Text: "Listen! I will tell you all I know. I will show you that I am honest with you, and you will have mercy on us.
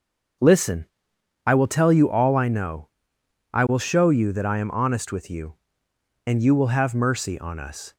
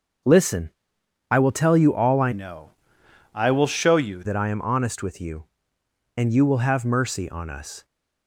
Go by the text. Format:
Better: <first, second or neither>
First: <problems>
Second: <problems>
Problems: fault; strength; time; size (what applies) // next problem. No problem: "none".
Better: first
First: starts louder than the rest; until 1.9 s; 6.5 dB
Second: starts louder than the rest; until 1.8 s; 6.5 dB // changes voice from "know" to "you"; from 2.3 to 4.2 s; 1.9 s long